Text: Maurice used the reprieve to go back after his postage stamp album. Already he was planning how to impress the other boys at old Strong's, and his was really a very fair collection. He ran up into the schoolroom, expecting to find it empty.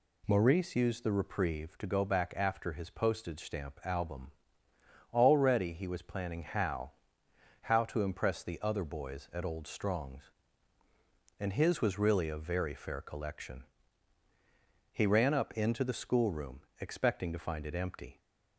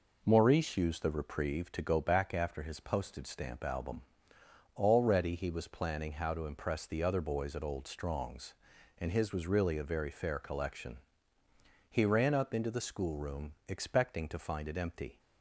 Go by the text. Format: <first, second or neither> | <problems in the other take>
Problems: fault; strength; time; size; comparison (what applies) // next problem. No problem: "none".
second | says "how" twice; at 7.6 s